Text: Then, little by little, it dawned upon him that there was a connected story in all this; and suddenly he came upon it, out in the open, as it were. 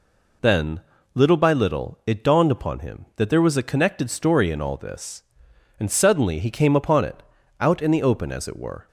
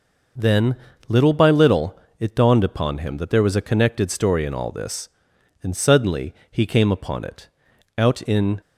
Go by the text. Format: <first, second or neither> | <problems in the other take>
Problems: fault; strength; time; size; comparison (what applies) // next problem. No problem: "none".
first | pauses between "suddenly" and "he"; slight; at 6.3 s; 0.16 s long // stops before "the open as it were"; at 8.6 s